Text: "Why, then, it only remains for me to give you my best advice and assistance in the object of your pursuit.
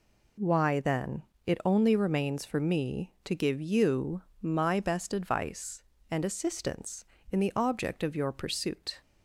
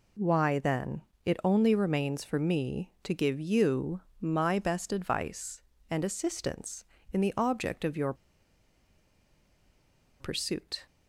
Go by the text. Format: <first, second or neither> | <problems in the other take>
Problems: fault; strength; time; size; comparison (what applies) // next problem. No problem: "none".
first | pauses between "you" and "my"; slight; at 3.9 s; 0.20 s long; slight in the first // pauses between "your" and "pursuit"; strong; at 8.1 s; 2.0 s long